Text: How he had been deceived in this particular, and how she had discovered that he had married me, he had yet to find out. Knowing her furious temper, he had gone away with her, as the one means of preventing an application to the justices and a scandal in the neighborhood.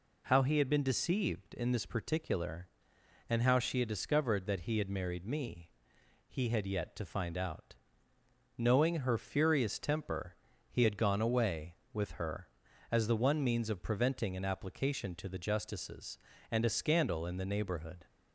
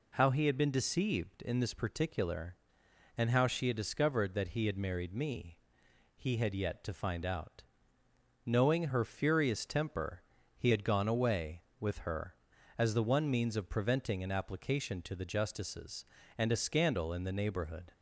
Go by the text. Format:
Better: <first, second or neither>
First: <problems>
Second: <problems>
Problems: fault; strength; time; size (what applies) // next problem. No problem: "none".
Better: neither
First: none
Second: none